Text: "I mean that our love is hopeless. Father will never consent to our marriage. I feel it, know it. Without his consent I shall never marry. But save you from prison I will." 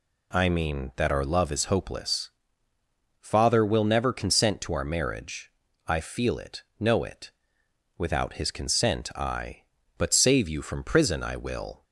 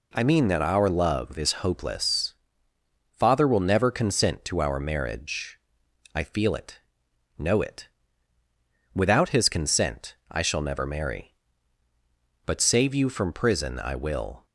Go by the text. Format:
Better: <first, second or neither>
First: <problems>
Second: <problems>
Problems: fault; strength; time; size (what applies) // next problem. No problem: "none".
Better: second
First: skips "shall never marry"; at 9.8 s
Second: none